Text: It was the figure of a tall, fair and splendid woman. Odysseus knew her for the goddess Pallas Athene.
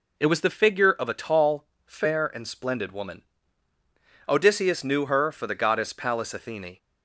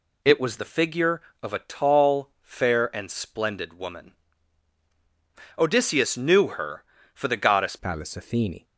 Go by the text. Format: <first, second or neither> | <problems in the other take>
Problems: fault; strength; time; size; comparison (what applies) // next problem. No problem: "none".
first | changes voice at "Pallas"; from 7.7 s on; 0.9 s long